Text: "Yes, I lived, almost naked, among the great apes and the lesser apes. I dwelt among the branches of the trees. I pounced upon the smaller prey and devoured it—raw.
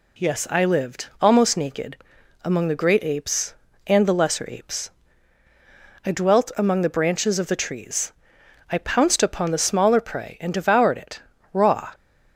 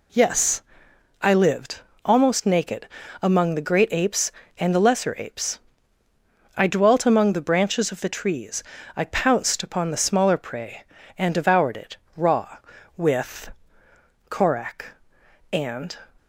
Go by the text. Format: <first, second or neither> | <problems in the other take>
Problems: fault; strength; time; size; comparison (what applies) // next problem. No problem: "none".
first | goes on to say "With Korak and"; strong; from 12.9 s on; 3.0 s long